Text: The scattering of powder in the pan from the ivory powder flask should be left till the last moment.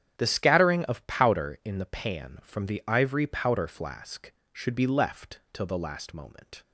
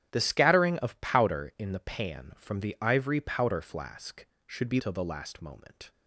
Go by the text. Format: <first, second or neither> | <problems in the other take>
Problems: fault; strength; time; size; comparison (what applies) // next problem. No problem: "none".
first | starts louder than the rest; strong; until 1.1 s; 10.5 dB; strong in the first // skips "left"; at 4.8 s